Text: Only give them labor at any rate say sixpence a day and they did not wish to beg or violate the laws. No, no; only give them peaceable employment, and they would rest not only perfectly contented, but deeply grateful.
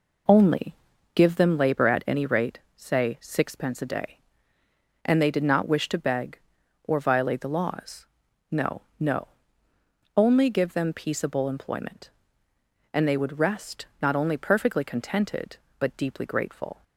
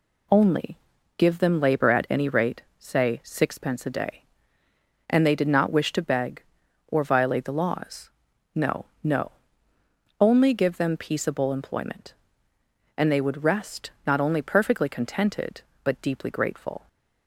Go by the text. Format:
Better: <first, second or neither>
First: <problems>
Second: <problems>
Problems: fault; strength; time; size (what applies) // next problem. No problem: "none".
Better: second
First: starts louder than the rest; noticeable; until 1.6 s; 4.5 dB // pauses between "Only" and "give"; at 0.7 s; 0.40 s long // pauses between "rate" and "say"; slight; at 2.5 s; 0.16 s long // pauses between "rest" and "not"; slight; at 13.8 s; 0.16 s long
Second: pauses between "Only" and "give"; at 0.7 s; 0.40 s long // pauses between "rate" and "say"; slight; at 2.6 s; 0.16 s long // pauses between "rest" and "not"; slight; at 13.8 s; 0.16 s long